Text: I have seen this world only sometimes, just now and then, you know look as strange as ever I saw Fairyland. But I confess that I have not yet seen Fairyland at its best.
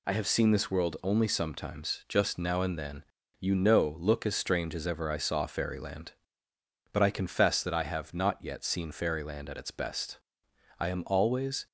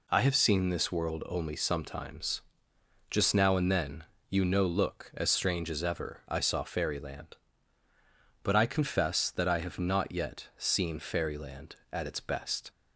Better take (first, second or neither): second